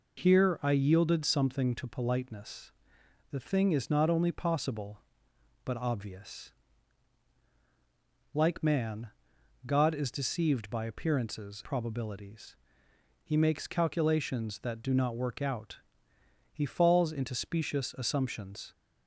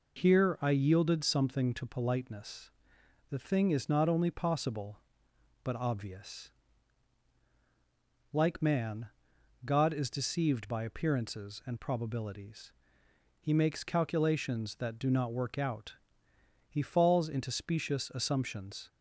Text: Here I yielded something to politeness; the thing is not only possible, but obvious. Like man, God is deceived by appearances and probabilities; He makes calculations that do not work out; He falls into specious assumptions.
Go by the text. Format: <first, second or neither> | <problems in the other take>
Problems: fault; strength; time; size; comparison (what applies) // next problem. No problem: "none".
second | skips "and"; at 11.6 s